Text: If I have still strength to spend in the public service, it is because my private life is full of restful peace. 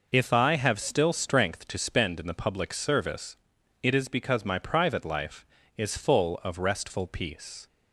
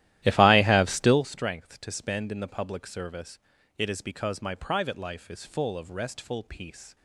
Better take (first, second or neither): first